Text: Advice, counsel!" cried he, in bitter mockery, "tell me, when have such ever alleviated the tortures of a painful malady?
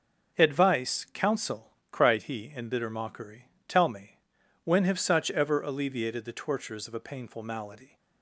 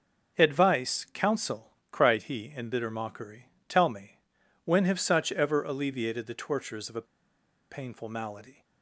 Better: first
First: starts louder than the rest; until 1.4 s; 7 dB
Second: starts louder than the rest; until 1.4 s; 7 dB // pauses between "a" and "painful"; noticeable; at 7.0 s; 0.67 s long

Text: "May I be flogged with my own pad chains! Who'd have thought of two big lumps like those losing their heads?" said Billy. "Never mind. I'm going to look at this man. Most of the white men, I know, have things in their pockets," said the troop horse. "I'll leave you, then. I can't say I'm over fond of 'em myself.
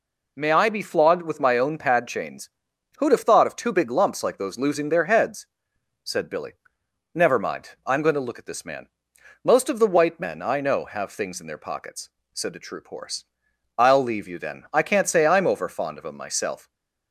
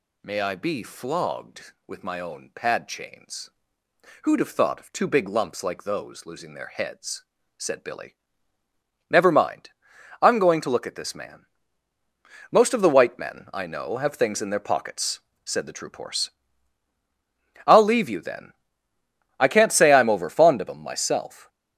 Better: neither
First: none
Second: none

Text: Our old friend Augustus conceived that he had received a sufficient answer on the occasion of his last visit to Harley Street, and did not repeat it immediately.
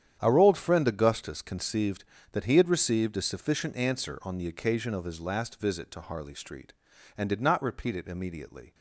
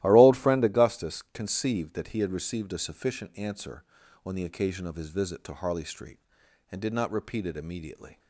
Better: first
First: starts louder than the rest; strong; until 1.2 s; 9.5 dB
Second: starts louder than the rest; strong; until 1.0 s; 15 dB // skips "last"; at 5.0 s

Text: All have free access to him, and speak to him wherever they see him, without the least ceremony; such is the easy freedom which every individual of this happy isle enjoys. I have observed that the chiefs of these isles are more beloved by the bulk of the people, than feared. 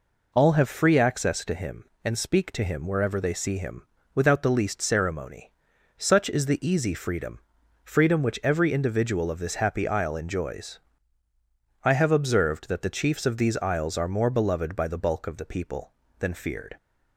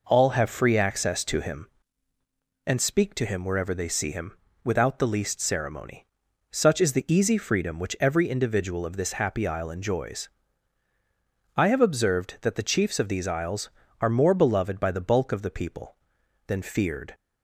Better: second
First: says "freedom" twice; at 7.8 s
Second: none

